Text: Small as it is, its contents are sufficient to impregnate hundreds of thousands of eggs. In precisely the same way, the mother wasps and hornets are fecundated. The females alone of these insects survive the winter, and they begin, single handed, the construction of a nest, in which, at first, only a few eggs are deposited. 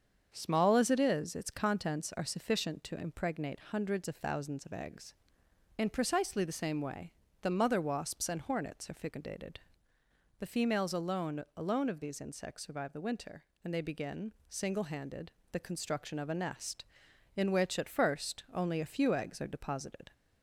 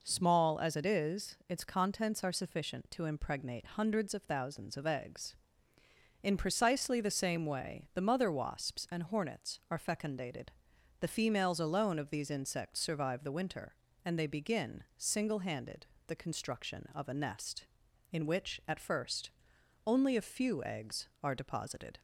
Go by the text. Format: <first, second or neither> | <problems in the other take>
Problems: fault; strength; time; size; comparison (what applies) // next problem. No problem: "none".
second | starts louder than the rest; until 1.3 s; 7 dB // says "alone" twice; at 11.5 s